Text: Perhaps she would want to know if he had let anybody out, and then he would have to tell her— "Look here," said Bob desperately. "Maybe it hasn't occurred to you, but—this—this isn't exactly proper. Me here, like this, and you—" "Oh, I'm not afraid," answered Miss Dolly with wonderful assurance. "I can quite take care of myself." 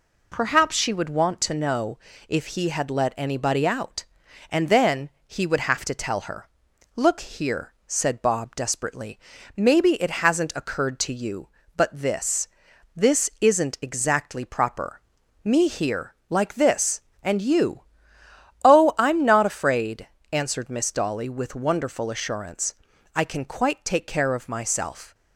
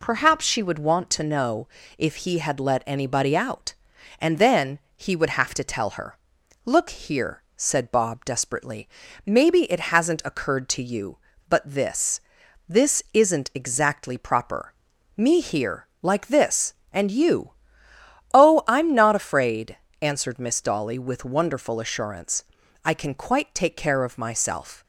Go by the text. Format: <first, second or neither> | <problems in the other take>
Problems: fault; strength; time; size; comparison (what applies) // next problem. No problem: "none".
neither | pauses between "know" and "if"; slight; the same in both // pauses between "then" and "he"; slight; the same in both